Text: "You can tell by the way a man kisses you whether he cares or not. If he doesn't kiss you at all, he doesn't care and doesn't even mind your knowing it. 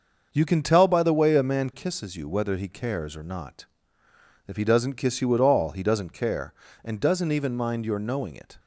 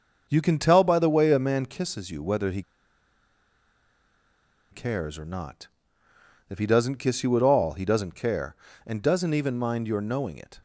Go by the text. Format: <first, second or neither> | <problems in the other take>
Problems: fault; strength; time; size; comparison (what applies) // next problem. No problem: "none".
first | starts louder than the rest; until 1.3 s; 6.5 dB; also in the first // pauses between "he" and "cares"; strong; at 2.6 s; 2.1 s long